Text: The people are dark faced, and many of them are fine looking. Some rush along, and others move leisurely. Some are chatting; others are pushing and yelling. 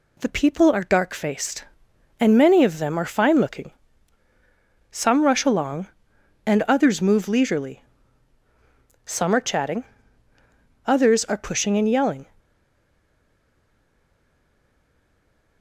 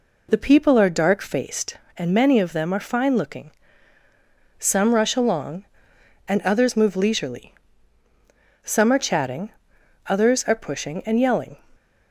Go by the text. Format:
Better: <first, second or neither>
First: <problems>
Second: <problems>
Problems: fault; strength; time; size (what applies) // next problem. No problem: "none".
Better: second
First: stays silent after the last word; strong; from 12.3 s on; 3.3 s long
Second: none